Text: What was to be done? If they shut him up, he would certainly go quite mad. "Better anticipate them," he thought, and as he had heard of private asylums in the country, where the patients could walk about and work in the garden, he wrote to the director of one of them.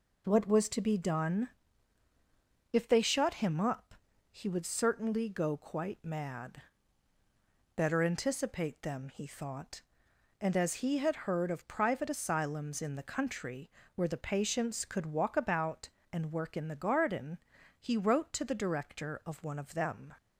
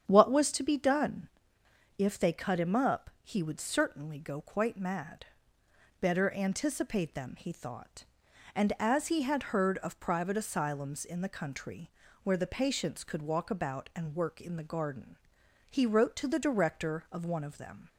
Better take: first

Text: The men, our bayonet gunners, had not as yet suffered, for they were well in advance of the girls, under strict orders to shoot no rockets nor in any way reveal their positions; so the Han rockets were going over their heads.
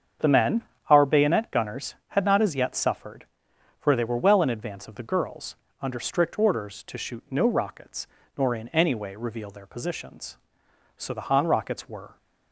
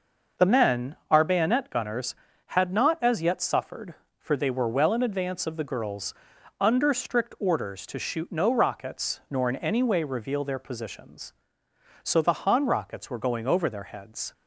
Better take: second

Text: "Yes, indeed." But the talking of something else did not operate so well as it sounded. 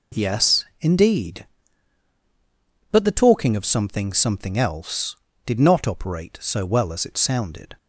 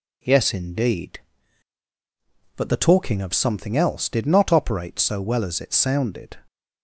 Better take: second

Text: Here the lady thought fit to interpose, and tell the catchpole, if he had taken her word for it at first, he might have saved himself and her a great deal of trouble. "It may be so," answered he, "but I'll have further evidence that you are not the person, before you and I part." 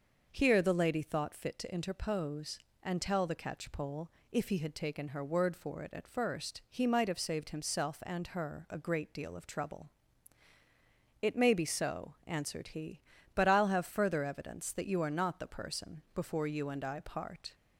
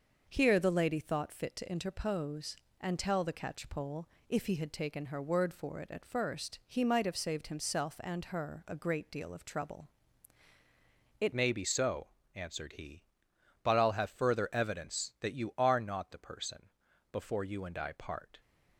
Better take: first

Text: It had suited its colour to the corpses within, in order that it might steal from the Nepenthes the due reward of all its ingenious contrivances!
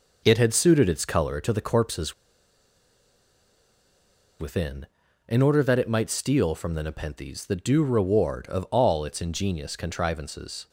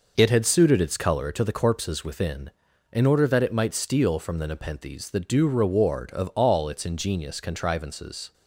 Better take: second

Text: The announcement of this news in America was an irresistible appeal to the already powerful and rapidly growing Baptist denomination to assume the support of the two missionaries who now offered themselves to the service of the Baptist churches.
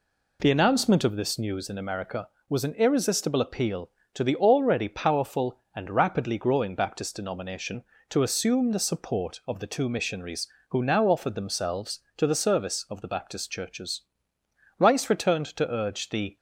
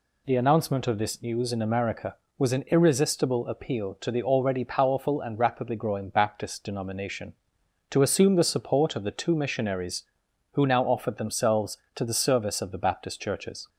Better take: second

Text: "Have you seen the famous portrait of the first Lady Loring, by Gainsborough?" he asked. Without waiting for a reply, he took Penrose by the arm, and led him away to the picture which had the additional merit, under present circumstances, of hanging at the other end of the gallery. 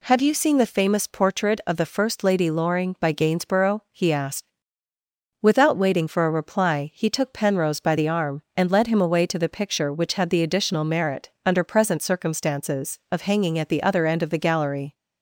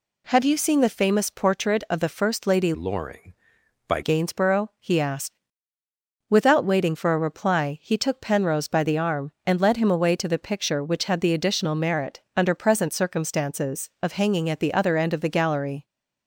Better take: first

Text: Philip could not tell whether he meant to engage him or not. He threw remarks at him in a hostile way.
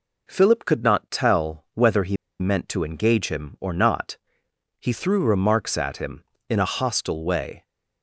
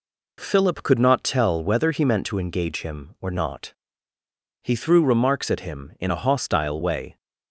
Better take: second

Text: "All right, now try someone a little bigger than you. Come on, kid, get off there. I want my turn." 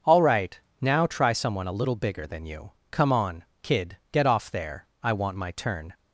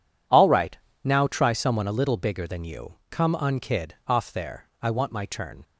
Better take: first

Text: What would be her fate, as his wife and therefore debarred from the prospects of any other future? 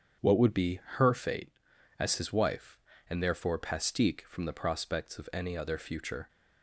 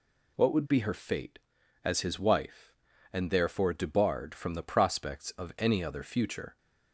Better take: second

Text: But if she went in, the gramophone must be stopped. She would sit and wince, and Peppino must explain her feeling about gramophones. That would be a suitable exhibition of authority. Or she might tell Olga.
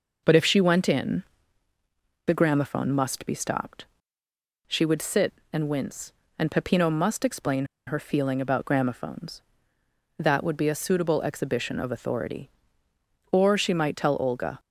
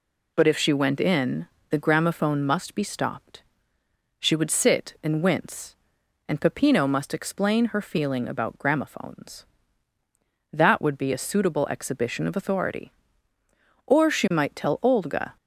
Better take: second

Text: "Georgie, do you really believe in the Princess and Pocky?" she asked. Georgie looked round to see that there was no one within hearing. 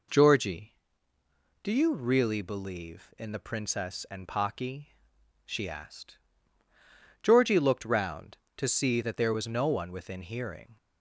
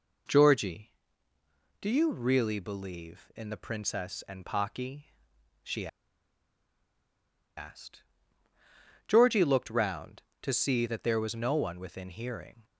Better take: first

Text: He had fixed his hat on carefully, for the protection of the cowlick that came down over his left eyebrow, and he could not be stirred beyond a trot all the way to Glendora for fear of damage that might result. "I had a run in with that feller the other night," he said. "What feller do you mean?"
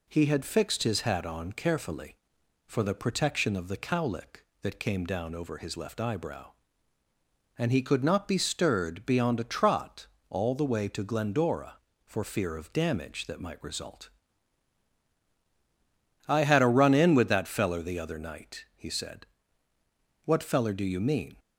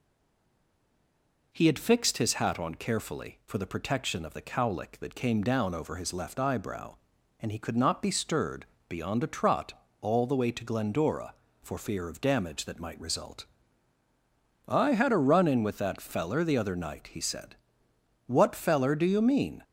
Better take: first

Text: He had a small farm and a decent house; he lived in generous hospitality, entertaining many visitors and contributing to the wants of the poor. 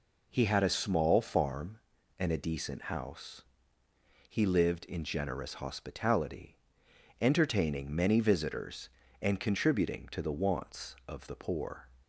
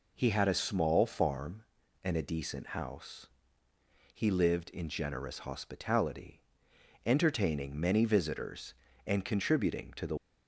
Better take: first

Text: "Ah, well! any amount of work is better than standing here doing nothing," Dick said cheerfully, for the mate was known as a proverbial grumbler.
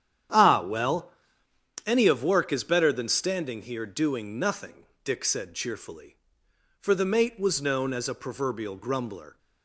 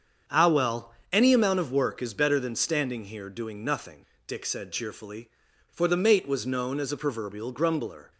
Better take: second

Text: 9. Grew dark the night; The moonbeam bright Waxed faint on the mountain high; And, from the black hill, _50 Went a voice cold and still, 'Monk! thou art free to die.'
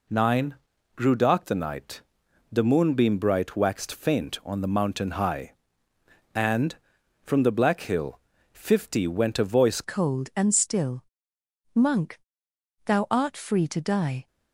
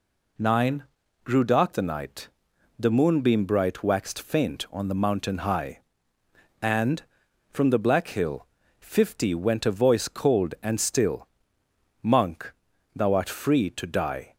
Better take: second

